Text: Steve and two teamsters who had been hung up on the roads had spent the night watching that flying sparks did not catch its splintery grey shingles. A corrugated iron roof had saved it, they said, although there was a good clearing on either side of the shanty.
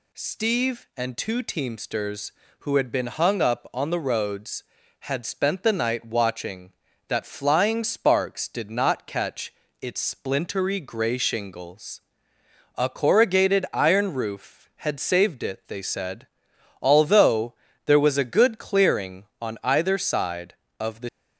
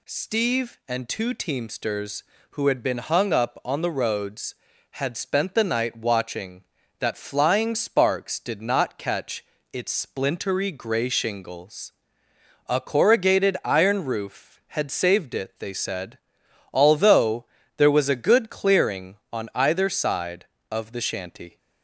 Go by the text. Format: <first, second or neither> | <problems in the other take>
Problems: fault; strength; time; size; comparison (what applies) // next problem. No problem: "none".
second | pauses between "catch" and "its"; slight; at 9.5 s; 0.28 s long; slight in the second // pauses between "although" and "there"; slight; at 17.5 s; 0.32 s long; slight in the second // stops before "shanty"; at 21.0 s